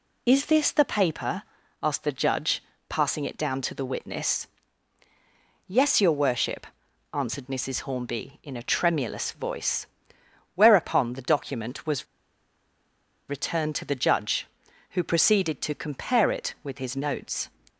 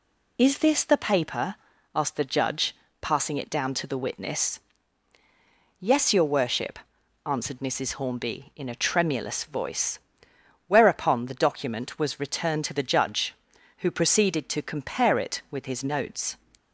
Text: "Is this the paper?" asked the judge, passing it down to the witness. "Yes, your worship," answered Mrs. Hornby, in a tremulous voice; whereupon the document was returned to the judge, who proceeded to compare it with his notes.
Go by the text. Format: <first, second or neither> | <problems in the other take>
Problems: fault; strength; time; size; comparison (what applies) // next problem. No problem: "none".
second | pauses between "was" and "returned"; at 12.0 s; 1.2 s long